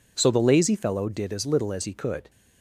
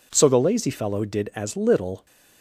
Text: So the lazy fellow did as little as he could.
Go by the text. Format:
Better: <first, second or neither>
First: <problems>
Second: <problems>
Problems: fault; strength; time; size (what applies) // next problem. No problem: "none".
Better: first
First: none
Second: stops before "as he could"; at 2.0 s